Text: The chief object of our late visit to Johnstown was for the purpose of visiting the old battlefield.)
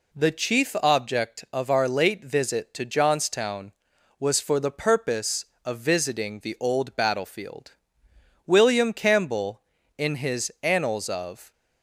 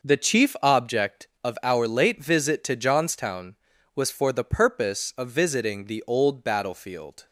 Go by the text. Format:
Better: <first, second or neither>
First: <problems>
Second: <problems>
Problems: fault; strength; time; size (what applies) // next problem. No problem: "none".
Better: second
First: goes on to say "William Campbell in his Annals of"; strong; from 8.4 s on; 3.0 s long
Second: none